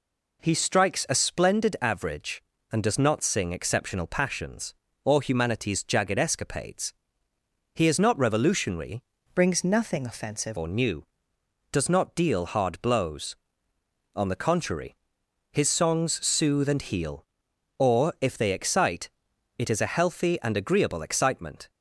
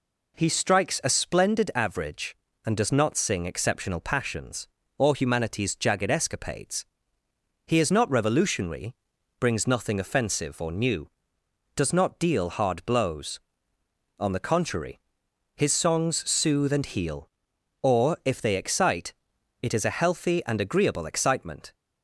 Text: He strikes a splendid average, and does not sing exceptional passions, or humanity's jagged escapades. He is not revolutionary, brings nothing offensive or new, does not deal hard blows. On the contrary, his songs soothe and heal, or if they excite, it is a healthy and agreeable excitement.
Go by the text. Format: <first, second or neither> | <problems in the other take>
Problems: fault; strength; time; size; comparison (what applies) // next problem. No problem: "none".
second | changes voice from "brings" to "offensive"; from 9.3 to 10.5 s; 1.2 s long